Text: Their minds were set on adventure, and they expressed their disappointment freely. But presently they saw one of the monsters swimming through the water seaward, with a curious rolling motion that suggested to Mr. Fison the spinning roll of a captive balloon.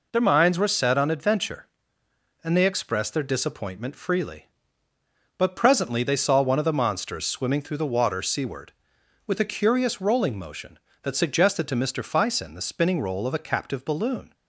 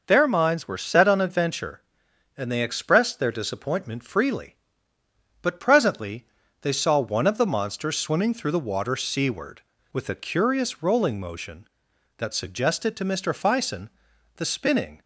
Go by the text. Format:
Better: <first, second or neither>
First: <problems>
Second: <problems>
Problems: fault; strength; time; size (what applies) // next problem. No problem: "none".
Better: first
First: none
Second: pauses between "presently" and "they"; slight; at 6.2 s; 0.34 s long // pauses between "Fison" and "the"; noticeable; at 13.8 s; 0.48 s long // stops before "roll of a captive balloon"; at 15.0 s